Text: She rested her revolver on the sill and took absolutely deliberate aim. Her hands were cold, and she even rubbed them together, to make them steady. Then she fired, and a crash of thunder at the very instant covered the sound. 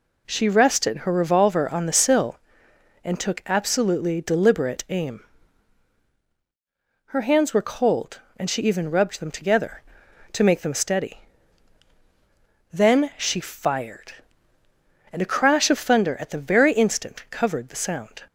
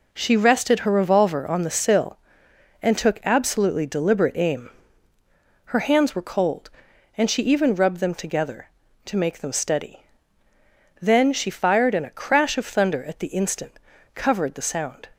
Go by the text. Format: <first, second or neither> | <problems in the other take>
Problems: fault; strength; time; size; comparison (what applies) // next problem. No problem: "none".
first | skips "very"; at 13.2 s // pauses between "instant" and "covered"; slight; at 13.7 s; 0.36 s long